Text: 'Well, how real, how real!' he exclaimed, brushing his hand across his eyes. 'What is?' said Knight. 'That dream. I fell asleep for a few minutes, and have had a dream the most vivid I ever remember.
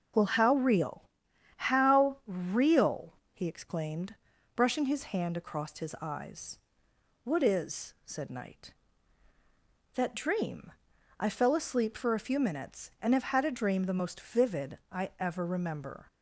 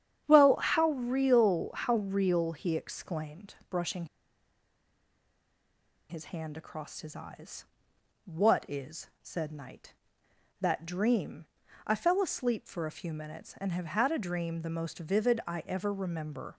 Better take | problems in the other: first | starts louder than the rest; strong; until 1.2 s; 9 dB // pauses between "brushing" and "his"; strong; at 4.0 s; 2.0 s long

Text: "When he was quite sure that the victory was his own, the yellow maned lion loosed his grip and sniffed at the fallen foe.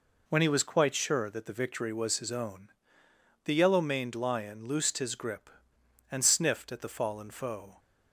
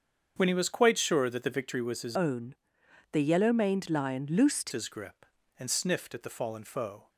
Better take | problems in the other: first | starts louder than the rest; strong; until 1.3 s; 7 dB // changes voice from "own" to "loosed"; from 2.1 to 4.7 s; 2.6 s long

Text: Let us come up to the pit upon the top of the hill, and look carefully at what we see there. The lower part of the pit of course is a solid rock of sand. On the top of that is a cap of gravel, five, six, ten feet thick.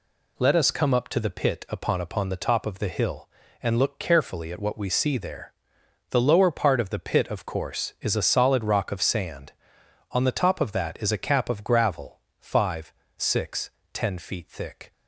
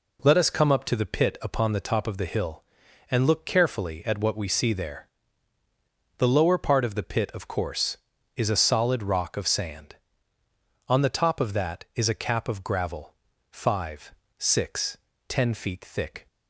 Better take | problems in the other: second | says "upon" twice; at 2.0 s

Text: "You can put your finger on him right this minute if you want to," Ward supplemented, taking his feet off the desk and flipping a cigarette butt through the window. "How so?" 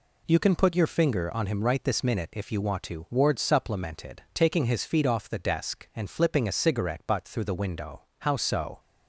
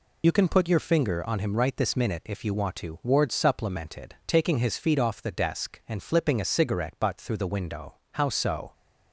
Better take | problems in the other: first | loses the start of "You"; at 0.2 s; 75 ms

